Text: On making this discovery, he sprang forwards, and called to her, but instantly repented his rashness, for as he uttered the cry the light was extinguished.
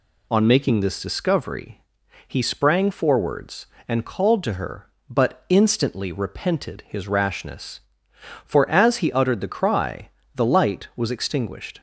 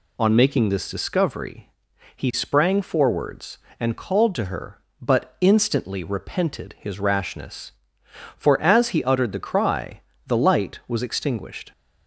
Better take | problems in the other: neither | pauses between "cry" and "the"; slight; the same in both

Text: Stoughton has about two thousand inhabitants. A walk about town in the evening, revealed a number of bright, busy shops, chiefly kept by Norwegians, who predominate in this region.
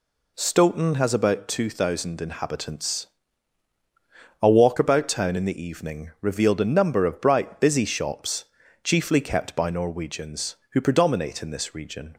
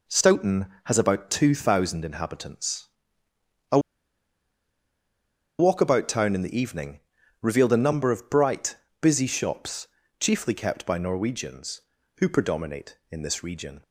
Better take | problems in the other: first | pauses between "A" and "walk"; strong; at 3.7 s; 1.8 s long

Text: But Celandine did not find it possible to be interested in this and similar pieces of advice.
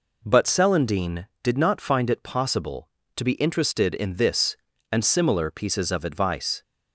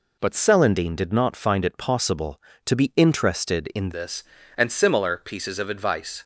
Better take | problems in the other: first | changes voice at "this"; from 3.9 s on; 2.3 s long

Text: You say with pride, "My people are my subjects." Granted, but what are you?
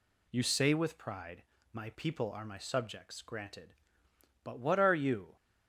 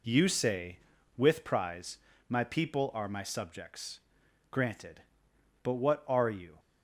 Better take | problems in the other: first | says "prize" for "pride"; at 1.4 s

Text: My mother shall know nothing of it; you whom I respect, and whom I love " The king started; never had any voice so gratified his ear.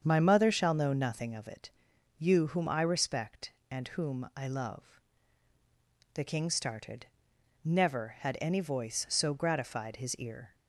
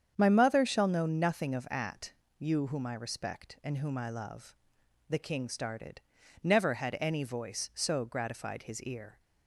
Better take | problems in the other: first | starts louder than the rest; strong; until 1.1 s; 8 dB; strong in the first // says "at" for "it"; at 1.6 s

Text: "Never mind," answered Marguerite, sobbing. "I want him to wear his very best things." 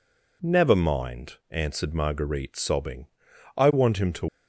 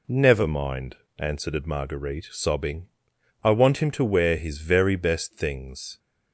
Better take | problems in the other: second | stops before "wear his very best things"; at 4.2 s

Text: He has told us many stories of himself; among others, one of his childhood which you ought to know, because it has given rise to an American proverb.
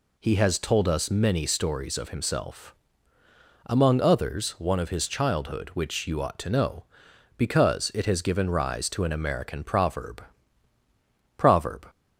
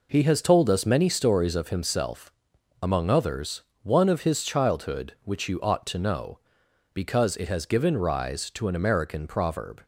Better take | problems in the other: second | says "proverb" twice; at 11.3 s

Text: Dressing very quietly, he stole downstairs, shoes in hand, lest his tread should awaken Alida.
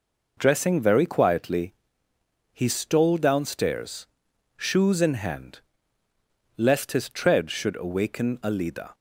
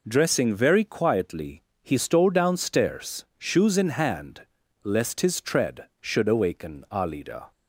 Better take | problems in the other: neither | none

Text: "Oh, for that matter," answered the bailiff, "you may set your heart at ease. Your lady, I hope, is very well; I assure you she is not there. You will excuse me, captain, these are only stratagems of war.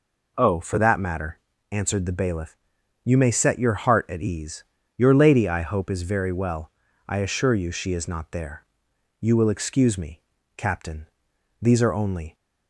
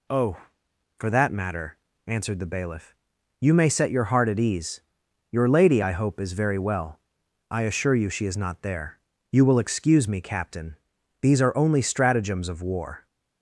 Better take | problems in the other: second | stops before "stratagems of war"; at 12.3 s

